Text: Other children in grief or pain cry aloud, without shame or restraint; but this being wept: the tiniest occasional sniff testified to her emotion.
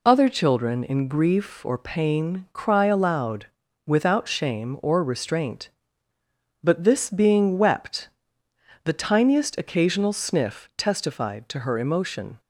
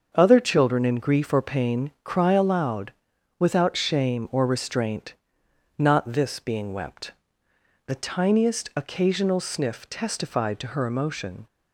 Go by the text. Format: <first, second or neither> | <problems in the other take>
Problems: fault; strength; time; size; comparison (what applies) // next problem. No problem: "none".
first | starts louder than the rest; until 1.1 s; 6.5 dB // says "not" for "but"; at 5.7 s